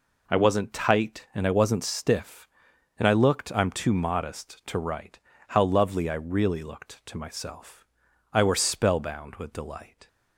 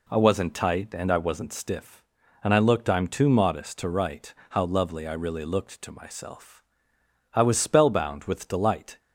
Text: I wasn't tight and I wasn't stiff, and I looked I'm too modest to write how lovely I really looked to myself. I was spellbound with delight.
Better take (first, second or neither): second